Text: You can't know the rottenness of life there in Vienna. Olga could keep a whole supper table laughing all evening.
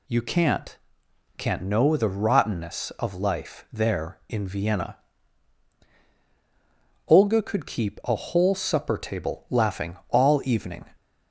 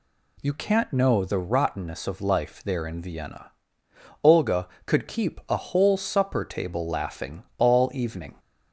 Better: second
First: says "can't" twice; at 1.3 s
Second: none

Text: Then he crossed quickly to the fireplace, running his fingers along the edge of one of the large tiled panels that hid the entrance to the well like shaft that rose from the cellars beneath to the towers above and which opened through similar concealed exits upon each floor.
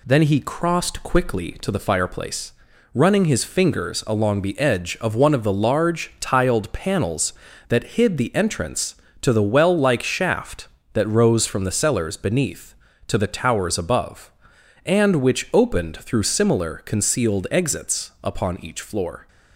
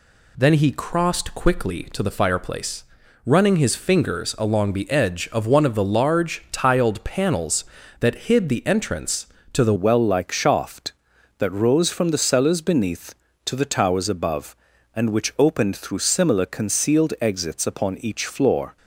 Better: first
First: none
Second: changes voice at "well"; from 9.7 s on; 9.0 s long

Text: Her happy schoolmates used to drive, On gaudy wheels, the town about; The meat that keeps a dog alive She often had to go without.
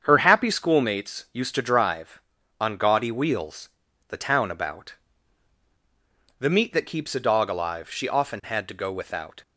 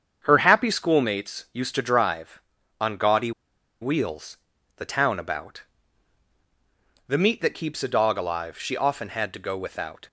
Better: first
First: starts louder than the rest; strong; until 1.0 s; 7.5 dB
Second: starts louder than the rest; strong; until 1.2 s; 7.5 dB // pauses between "gaudy" and "wheels"; noticeable; at 3.3 s; 0.50 s long

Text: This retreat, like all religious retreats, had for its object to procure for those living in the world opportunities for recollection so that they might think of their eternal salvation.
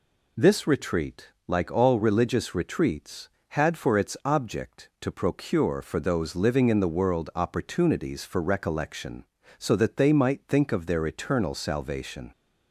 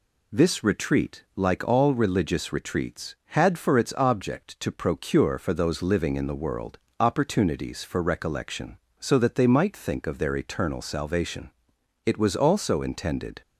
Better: first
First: none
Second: pauses between "world" and "opportunities"; slight; at 6.7 s; 0.22 s long // goes on to say "It was also intended"; from 12.0 s on; 1.3 s long

